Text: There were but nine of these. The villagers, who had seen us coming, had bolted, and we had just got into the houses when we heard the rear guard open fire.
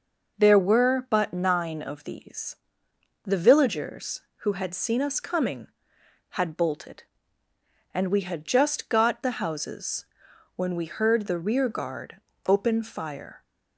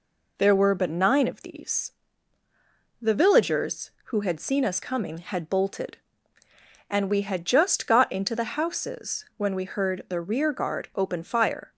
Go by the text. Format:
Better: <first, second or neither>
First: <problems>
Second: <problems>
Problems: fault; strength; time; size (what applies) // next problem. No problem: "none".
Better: second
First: skips "into"; at 9.2 s // pauses between "houses" and "when"; noticeable; at 10.0 s; 0.52 s long // pauses between "guard" and "open"; slight; at 12.1 s; 0.30 s long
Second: none